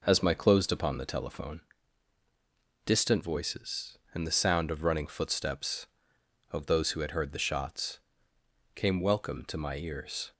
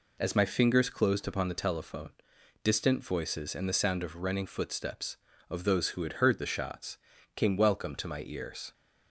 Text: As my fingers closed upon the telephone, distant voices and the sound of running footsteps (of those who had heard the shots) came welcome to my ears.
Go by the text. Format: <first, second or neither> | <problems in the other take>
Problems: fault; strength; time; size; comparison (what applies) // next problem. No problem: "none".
second | skips "fingers"; at 0.3 s